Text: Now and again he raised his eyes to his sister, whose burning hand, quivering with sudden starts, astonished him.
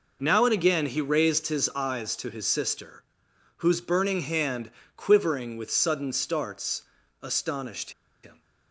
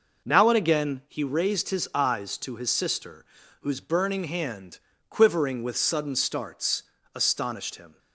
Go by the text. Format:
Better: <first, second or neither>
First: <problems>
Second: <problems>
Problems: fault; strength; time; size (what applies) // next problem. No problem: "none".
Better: second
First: pauses between "astonished" and "him"; slight; at 7.9 s; 0.32 s long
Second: none